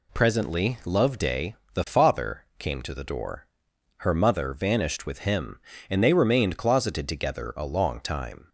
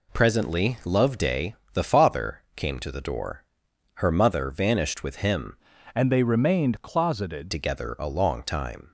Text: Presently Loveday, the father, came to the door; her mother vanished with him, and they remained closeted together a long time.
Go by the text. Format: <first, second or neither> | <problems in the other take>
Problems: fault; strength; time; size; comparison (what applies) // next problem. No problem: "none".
first | changes voice from "and" to "closeted"; from 5.9 to 7.5 s; 1.6 s long